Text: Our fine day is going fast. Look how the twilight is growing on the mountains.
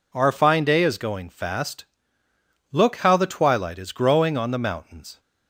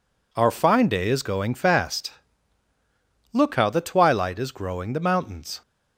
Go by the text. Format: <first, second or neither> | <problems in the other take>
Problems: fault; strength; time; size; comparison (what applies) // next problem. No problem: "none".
first | skips "on"; at 4.9 s